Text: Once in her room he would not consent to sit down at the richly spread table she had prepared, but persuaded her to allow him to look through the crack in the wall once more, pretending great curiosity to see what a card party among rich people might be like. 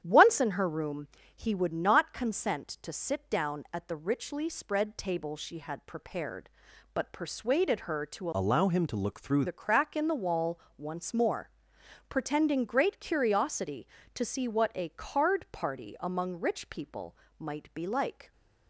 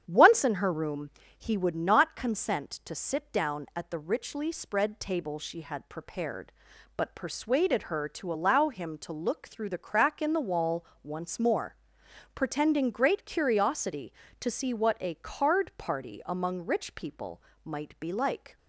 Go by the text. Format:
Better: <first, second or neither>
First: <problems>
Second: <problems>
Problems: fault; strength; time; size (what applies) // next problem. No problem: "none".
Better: second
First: starts louder than the rest; strong; until 1.0 s; 10 dB // pauses between "room" and "he"; slight; at 1.0 s; 0.30 s long // changes voice from "allow" to "through"; from 8.3 to 9.4 s; 1.1 s long // pauses between "wall" and "once"; slight; at 10.5 s; 0.20 s long // pauses between "people" and "might"; slight; at 17.1 s; 0.22 s long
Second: starts louder than the rest; strong; until 1.0 s; 9 dB // pauses between "room" and "he"; slight; at 1.0 s; 0.30 s long // pauses between "wall" and "once"; slight; at 10.8 s; 0.20 s long // pauses between "people" and "might"; slight; at 17.4 s; 0.22 s long